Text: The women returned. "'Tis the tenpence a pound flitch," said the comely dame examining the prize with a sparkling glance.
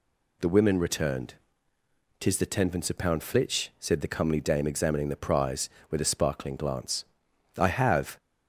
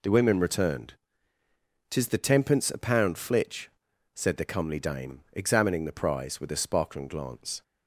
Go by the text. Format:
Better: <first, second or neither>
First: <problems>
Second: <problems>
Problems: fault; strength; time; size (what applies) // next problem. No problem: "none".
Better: second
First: goes on to say "I have"; from 7.5 s on; 0.60 s long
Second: none